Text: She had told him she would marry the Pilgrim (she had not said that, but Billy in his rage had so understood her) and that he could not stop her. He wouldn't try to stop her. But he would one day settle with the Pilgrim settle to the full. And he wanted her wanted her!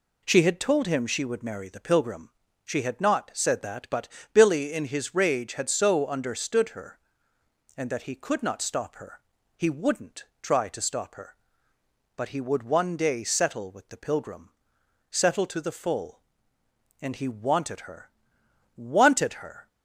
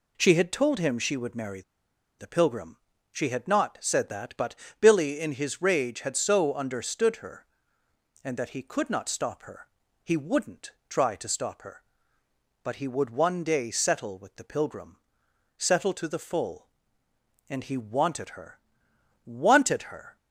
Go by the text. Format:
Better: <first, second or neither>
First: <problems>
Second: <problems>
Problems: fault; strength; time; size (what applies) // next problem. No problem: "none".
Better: first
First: pauses between "but" and "Billy"; slight; at 4.0 s; 0.26 s long // pauses between "wouldn't" and "try"; slight; at 10.2 s; 0.16 s long // pauses between "Pilgrim" and "settle"; noticeable; at 14.5 s; 0.60 s long // pauses between "her" and "wanted"; noticeable; at 18.1 s; 0.66 s long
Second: pauses between "marry" and "the"; noticeable; at 1.6 s; 0.57 s long // pauses between "but" and "Billy"; slight; at 4.5 s; 0.26 s long // pauses between "wouldn't" and "try"; slight; at 10.7 s; 0.16 s long // pauses between "Pilgrim" and "settle"; noticeable; at 14.9 s; 0.60 s long // pauses between "her" and "wanted"; noticeable; at 18.5 s; 0.66 s long